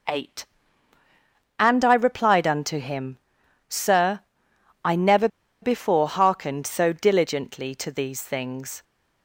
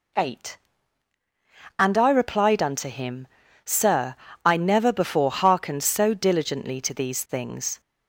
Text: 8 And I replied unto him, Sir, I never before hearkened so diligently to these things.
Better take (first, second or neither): second